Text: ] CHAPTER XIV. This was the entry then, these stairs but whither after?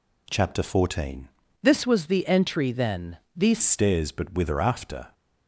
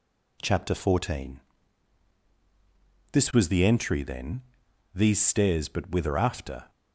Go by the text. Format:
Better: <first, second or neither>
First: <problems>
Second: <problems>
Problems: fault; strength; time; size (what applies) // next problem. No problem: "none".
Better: second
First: changes voice from "This" to "these"; from 1.6 to 3.6 s; 2.0 s long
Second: none